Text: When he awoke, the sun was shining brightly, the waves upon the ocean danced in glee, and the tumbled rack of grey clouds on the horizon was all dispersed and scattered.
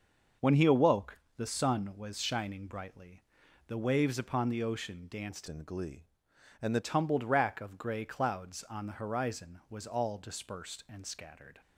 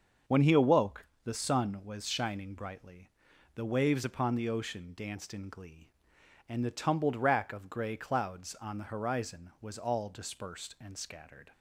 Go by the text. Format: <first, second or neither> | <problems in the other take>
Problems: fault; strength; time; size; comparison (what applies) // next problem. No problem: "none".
second | starts louder than the rest; noticeable; until 1.5 s; 6 dB; also in the second // changes voice from "in" to "the"; from 5.4 to 6.7 s; 1.3 s long